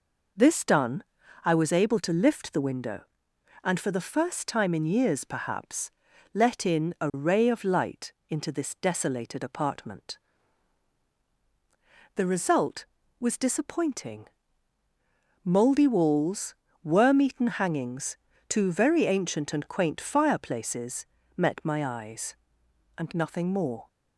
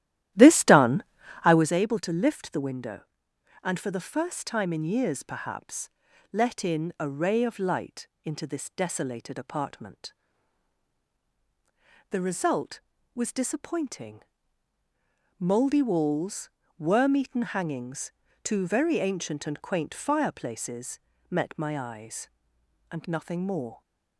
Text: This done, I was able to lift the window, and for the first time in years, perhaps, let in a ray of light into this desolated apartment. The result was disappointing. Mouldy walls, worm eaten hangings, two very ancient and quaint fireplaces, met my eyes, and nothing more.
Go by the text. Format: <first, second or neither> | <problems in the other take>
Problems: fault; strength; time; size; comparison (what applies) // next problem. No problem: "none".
first | starts louder than the rest; strong; until 1.8 s; 13 dB // pauses between "light" and "into"; slight; at 8.0 s; 0.16 s long; slight in the first